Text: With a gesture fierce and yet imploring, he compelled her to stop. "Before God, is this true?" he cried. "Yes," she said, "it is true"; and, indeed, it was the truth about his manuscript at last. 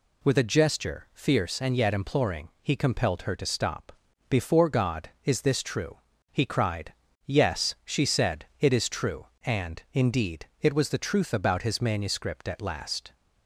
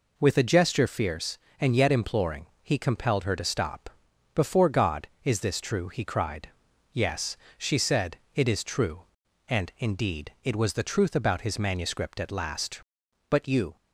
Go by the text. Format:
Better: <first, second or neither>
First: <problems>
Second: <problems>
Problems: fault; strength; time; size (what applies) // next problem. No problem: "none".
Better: first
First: none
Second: goes on to say "But you"; slight; from 13.2 s on; 0.46 s long